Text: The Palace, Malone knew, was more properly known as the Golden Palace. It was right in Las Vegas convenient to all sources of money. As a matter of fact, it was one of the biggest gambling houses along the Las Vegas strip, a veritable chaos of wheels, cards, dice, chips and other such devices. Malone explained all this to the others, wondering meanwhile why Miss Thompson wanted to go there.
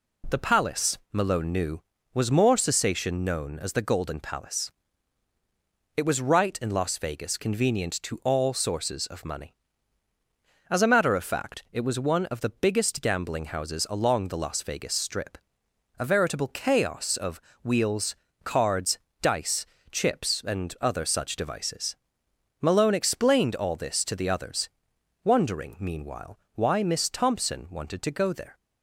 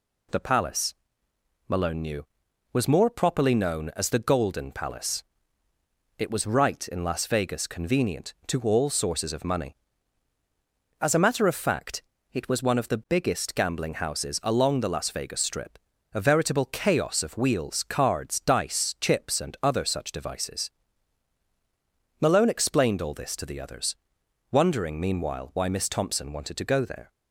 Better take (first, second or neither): second